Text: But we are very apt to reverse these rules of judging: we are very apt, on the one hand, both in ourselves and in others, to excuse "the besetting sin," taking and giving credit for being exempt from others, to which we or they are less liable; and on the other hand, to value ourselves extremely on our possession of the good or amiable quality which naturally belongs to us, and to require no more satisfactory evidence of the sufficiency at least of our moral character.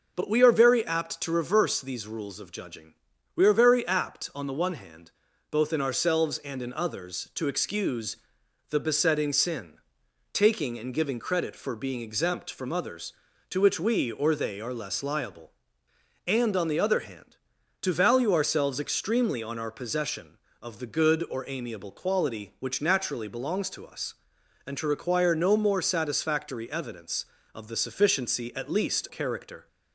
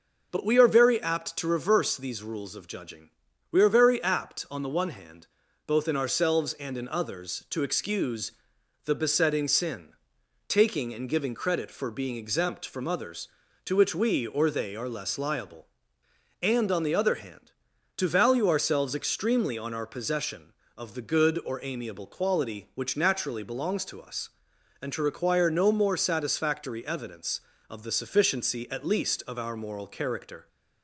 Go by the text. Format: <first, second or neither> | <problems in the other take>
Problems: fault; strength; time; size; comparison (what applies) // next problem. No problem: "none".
second | pauses between "excuse" and "the"; noticeable; at 8.1 s; 0.54 s long; noticeable in the second // skips "of our moral"; at 29.0 s